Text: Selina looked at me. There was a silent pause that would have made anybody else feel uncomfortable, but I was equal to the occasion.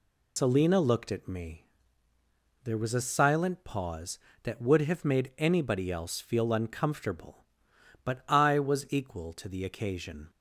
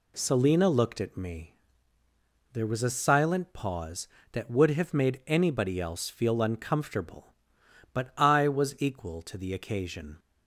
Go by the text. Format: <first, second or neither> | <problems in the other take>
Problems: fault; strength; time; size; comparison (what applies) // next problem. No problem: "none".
second | loses the start of "Selina"; at 0.3 s; 105 ms